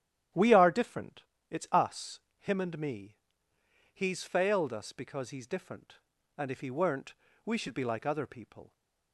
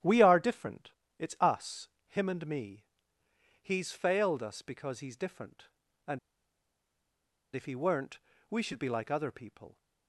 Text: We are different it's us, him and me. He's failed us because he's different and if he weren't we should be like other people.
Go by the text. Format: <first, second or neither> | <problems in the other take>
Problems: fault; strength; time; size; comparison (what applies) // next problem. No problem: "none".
first | starts louder than the rest; strong; until 1.2 s; 11 dB; strong in the first // pauses between "different" and "it's"; slight; at 0.9 s; 0.26 s long; slight in the first // pauses between "and" and "if"; strong; at 6.1 s; 1.3 s long // pauses between "weren't" and "we"; slight; at 8.1 s; 0.30 s long; slight in the first